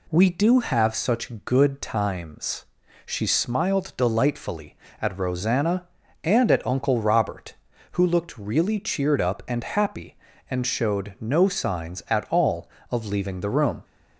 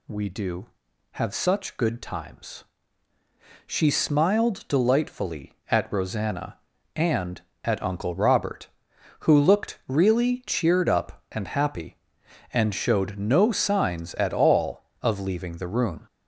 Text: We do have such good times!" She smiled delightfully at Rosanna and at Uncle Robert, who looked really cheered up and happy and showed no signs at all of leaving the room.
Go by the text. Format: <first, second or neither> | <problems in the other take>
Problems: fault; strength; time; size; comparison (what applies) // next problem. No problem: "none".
neither | none